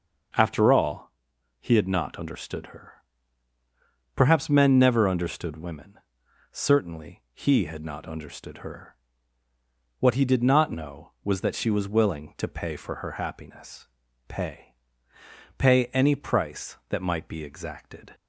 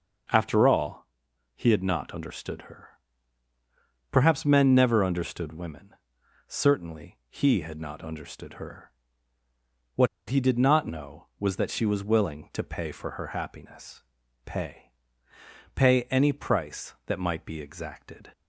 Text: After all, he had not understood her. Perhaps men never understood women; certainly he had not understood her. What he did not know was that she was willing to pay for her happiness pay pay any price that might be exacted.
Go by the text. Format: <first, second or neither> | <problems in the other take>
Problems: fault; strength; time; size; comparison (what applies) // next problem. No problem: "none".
first | starts louder than the rest; noticeable; until 1.8 s; 6 dB; noticeable in the first // pauses between "What" and "he"; slight; at 10.0 s; 0.21 s long // pauses between "happiness" and "pay"; at 14.0 s; 0.44 s long; also in the first // pauses between "pay" and "pay"; noticeable; at 14.9 s; 0.82 s long; noticeable in the first